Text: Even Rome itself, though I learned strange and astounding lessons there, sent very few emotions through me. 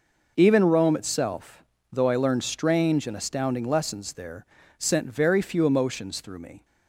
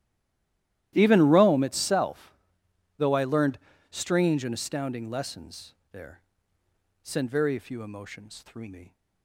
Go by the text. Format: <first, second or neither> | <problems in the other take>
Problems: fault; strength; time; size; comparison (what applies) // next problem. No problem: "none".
first | stays silent before the first word; slight; until 0.9 s; 0.9 s long // starts louder than the rest; strong; until 1.9 s; 13.5 dB // pauses between "learned" and "strange"; slight; at 3.5 s; 0.32 s long // pauses between "lessons" and "there"; slight; at 5.7 s; 0.18 s long